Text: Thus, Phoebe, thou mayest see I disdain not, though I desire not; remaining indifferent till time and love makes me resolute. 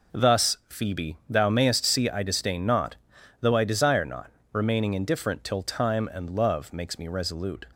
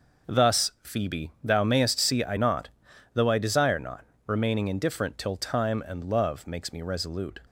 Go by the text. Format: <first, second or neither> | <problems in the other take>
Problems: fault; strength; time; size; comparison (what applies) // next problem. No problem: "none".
first | skips "disdain"; at 2.3 s